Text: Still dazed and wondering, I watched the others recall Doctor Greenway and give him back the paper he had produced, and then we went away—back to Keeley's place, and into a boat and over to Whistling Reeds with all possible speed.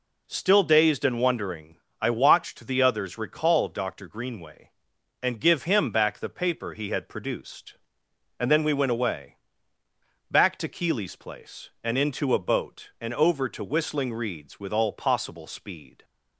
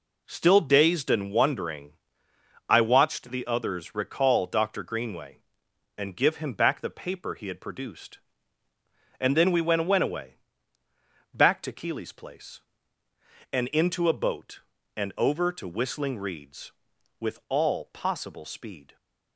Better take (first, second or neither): first